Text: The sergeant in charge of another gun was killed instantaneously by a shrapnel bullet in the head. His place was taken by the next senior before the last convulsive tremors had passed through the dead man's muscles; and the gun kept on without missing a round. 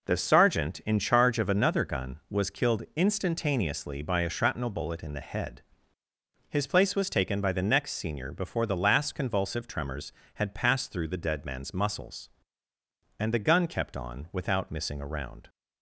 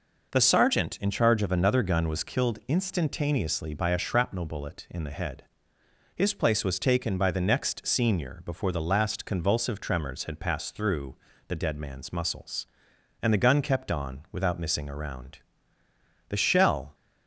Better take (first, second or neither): first